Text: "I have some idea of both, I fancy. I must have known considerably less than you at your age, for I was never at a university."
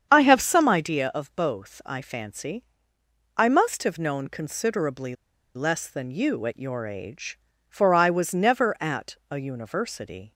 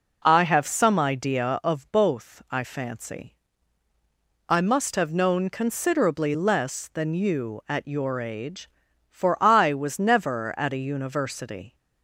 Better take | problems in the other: second | starts louder than the rest; strong; until 1.1 s; 8 dB // pauses between "considerably" and "less"; at 5.1 s; 0.40 s long

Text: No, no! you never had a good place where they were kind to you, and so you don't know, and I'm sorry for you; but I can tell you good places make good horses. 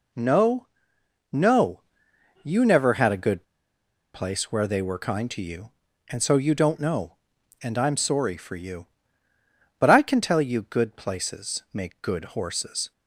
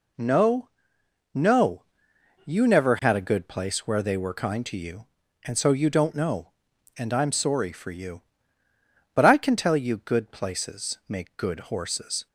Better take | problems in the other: second | pauses between "good" and "place"; noticeable; at 3.4 s; 0.71 s long

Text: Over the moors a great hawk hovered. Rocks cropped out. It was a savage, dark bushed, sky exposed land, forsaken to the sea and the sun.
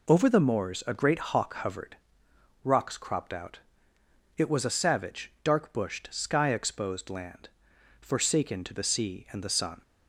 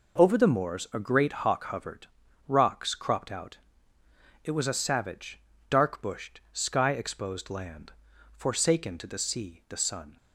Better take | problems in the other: first | skips "and"; at 9.6 s

